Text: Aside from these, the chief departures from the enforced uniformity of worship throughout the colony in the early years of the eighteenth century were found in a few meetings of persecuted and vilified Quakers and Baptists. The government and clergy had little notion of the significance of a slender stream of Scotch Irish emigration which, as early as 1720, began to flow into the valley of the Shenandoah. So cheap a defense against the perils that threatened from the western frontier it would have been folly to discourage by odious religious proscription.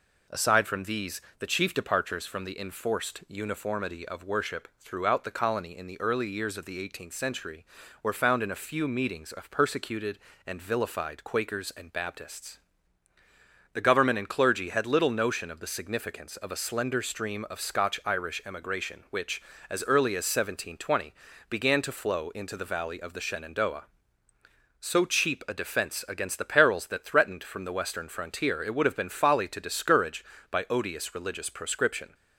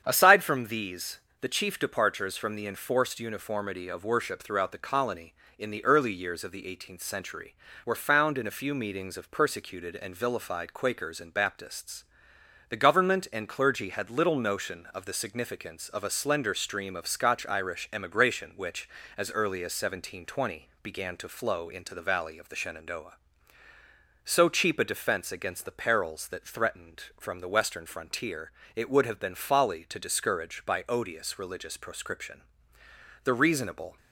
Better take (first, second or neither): first